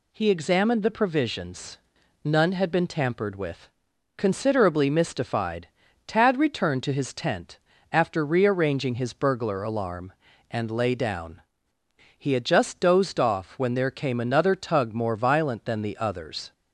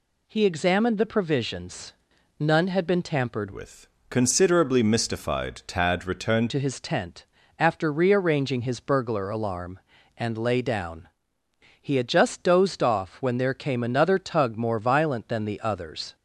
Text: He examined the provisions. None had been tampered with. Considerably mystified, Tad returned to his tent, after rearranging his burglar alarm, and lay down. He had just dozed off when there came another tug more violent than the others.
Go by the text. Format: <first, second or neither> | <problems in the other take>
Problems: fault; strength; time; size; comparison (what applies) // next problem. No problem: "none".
first | changes voice from "with" to "returned"; from 3.5 to 6.4 s; 2.9 s long